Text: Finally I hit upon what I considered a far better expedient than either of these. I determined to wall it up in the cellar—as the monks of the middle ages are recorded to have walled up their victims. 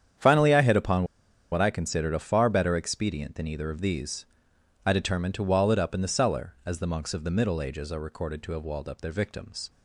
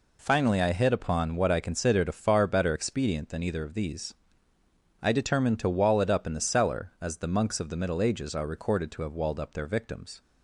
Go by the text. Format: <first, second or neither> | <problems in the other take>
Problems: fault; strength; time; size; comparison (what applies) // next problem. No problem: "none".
second | starts louder than the rest; strong; until 1.6 s; 9 dB // pauses between "upon" and "what"; noticeable; at 1.0 s; 0.47 s long